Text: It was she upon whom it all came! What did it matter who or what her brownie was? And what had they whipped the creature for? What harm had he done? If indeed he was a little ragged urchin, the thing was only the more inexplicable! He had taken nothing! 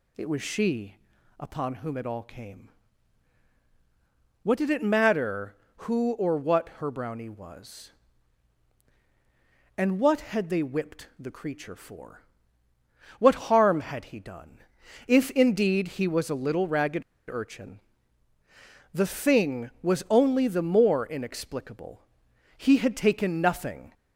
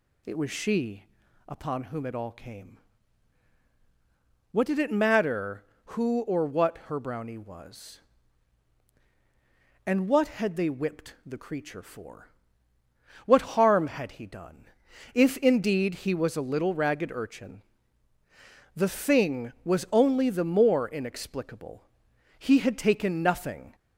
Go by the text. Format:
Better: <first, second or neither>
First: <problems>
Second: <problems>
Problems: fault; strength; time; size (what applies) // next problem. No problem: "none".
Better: second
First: pauses between "she" and "upon"; at 0.9 s; 0.42 s long // pauses between "ragged" and "urchin"; slight; at 17.0 s; 0.28 s long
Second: pauses between "she" and "upon"; at 1.0 s; 0.42 s long